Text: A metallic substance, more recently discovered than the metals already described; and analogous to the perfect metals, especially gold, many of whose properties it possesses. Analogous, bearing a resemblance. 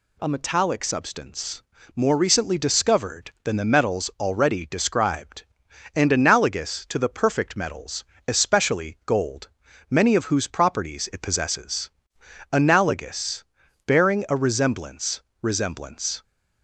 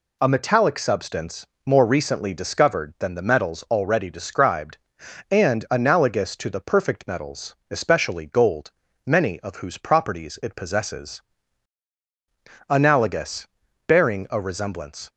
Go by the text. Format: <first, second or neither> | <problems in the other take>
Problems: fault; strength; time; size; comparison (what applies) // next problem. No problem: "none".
second | says "resemblance" twice; at 15.4 s